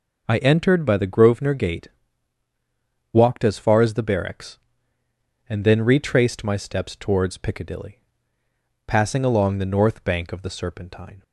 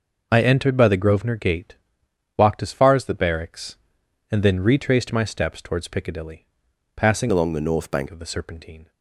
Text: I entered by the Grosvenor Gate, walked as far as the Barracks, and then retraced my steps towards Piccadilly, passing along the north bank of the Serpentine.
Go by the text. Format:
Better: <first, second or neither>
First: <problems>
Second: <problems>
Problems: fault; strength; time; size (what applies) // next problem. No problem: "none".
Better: first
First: none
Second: changes voice from "along" to "bank"; from 7.3 to 8.0 s; 0.7 s long